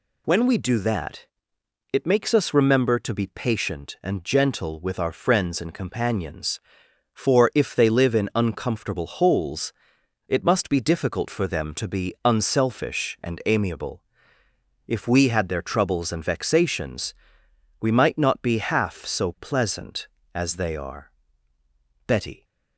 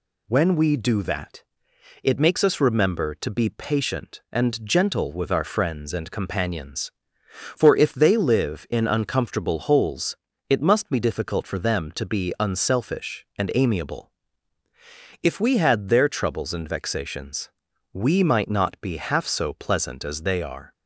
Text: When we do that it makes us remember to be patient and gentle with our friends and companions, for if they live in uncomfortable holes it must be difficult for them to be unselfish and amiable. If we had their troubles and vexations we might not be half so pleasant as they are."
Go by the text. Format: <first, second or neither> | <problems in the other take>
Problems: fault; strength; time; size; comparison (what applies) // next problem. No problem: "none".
second | pauses between "that" and "it"; noticeable; at 1.2 s; 0.66 s long; noticeable in the second // pauses between "holes" and "it"; noticeable; at 9.7 s; 0.56 s long; slight in the second // pauses between "vexations" and "we"; noticeable; at 17.1 s; 0.66 s long; also in the second // goes on to say "Betty"; slight; from 22.0 s on; 0.38 s long